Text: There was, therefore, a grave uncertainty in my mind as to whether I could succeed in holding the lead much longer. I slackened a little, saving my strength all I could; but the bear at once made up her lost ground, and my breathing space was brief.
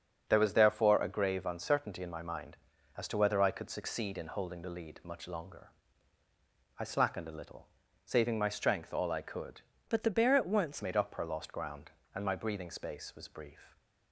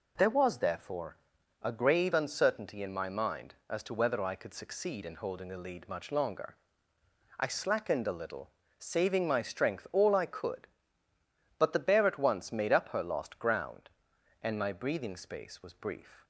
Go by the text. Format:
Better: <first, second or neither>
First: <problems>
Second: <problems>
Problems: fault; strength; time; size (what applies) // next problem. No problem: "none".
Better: second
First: starts louder than the rest; until 1.3 s; 7 dB // changes voice from "but" to "once"; from 9.8 to 10.8 s; 1.0 s long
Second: none